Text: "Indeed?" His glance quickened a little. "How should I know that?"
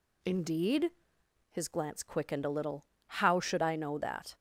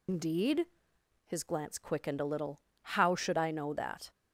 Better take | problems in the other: first | loses the start of "Indeed"; at 0.0 s; 100 ms

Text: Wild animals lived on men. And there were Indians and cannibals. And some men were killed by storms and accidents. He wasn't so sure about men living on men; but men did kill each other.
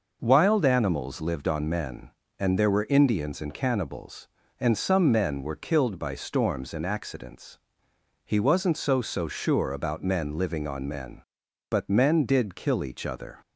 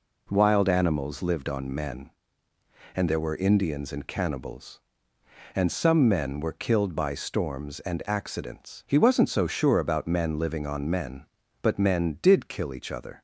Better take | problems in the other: second | says "so" twice; at 9.0 s

